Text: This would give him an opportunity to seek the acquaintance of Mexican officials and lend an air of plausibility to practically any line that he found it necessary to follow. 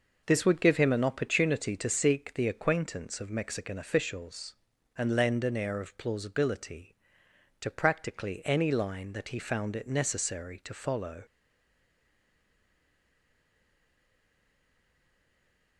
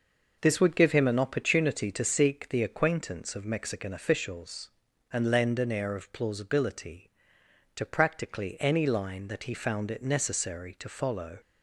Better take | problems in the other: second | stays silent after the last word; strong; from 11.2 s on; 4.5 s long

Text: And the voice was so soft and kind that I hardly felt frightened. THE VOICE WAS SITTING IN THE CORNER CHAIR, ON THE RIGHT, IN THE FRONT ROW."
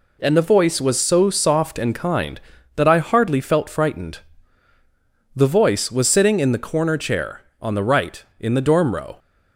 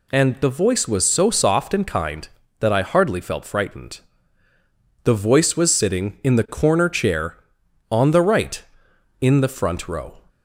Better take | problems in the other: second | says "Dorm" for "FRONT"; at 8.6 s

